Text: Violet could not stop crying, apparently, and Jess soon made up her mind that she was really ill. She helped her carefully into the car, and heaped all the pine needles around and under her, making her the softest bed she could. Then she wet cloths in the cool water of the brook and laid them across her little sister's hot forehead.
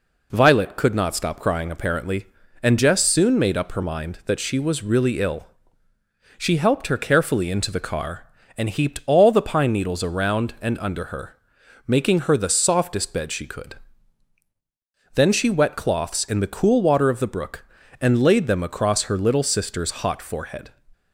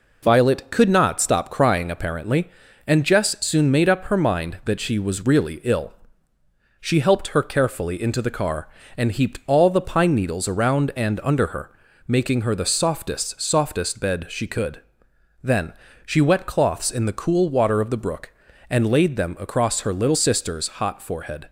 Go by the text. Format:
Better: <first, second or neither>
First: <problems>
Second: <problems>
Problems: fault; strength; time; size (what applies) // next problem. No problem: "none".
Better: first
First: none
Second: says "softest" twice; at 13.3 s // pauses between "Then" and "she"; slight; at 15.7 s; 0.32 s long